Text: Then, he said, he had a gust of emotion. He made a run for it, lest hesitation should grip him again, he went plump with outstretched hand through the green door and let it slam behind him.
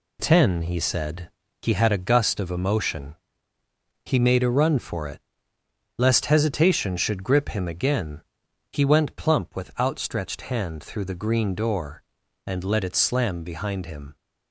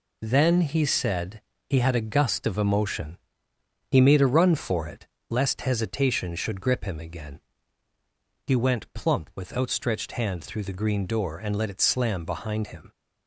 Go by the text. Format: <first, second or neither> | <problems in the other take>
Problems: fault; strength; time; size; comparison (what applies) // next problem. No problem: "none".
second | says "Ten" for "Then"; at 0.2 s